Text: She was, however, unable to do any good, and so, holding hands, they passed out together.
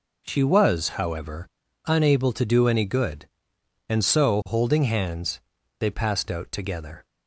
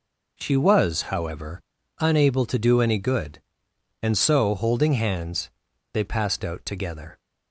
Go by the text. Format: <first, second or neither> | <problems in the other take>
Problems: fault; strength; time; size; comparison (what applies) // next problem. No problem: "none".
neither | none